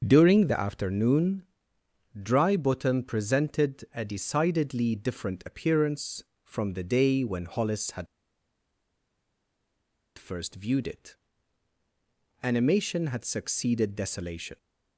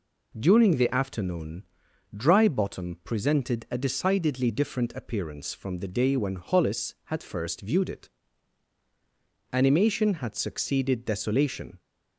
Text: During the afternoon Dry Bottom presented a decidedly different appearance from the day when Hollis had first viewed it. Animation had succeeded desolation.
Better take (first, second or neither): second